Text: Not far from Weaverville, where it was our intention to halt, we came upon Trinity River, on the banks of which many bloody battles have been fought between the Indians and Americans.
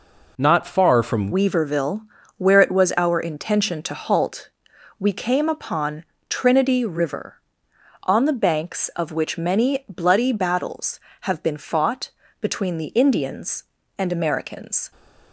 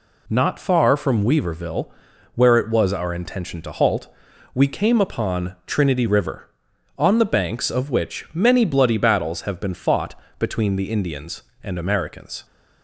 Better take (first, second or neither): second